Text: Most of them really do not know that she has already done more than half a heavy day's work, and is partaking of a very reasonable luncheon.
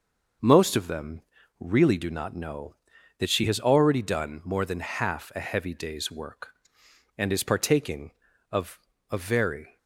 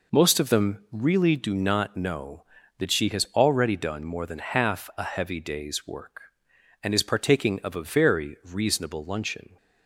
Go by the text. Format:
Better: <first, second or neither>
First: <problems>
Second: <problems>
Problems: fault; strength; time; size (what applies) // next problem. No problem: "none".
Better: second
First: pauses between "them" and "really"; at 1.2 s; 0.38 s long // pauses between "of" and "a"; slight; at 8.7 s; 0.30 s long // stops before "reasonable luncheon"; at 9.7 s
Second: none